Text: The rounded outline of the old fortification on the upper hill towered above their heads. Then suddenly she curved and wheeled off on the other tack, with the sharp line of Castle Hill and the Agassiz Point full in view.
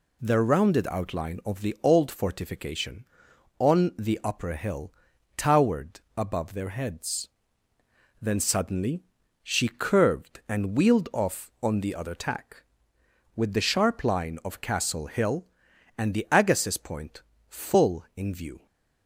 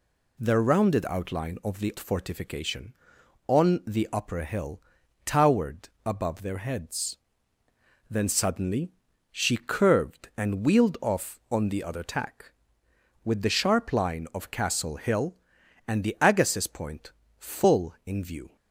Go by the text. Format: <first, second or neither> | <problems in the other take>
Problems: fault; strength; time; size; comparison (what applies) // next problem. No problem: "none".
first | skips "old"; at 1.9 s // pauses between "hill" and "towered"; noticeable; at 4.7 s; 0.46 s long; noticeable in the first // pauses between "towered" and "above"; slight; at 5.8 s; 0.16 s long; slight in the first // pauses between "suddenly" and "she"; at 8.9 s; 0.40 s long; also in the first // pauses between "Point" and "full"; slight; at 17.1 s; 0.28 s long; slight in the first